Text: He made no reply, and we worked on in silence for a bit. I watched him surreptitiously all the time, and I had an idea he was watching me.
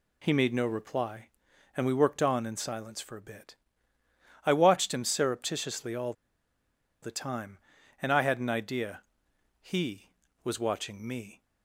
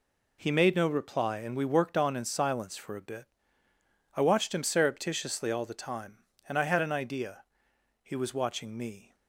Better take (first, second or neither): second